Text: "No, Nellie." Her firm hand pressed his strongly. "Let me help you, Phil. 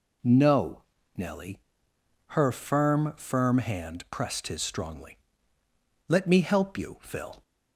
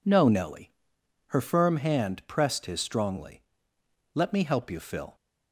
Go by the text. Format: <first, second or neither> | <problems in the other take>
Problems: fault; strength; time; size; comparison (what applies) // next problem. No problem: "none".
second | says "firm" twice; at 3.1 s